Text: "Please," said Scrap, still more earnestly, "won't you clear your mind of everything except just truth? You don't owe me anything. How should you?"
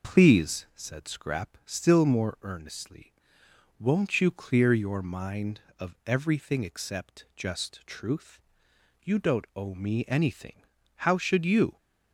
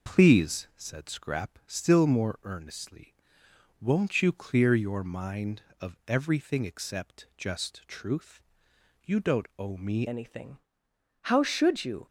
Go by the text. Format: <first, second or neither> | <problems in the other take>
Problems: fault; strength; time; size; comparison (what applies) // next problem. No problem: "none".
first | changes voice at "anything"; from 10.0 s on; 2.0 s long